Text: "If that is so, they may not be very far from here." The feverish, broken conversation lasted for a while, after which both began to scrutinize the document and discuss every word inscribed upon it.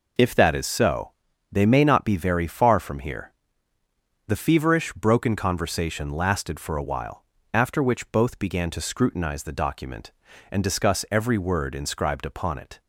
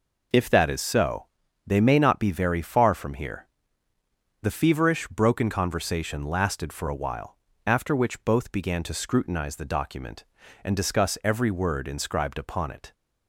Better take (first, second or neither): neither